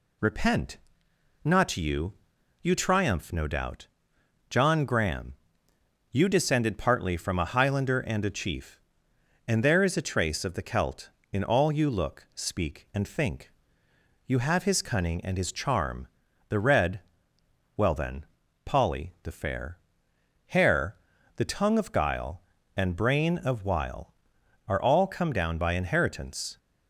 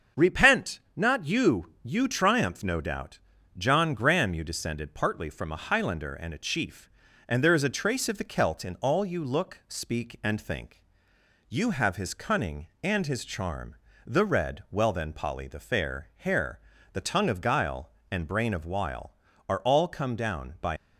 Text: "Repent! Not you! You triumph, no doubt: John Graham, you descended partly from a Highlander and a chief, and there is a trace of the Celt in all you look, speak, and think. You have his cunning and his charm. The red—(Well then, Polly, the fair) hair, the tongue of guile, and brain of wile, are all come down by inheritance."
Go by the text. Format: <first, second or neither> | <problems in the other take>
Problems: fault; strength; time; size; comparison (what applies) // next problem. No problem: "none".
first | starts louder than the rest; until 1.3 s; 7 dB // stops before "inheritance"; at 20.7 s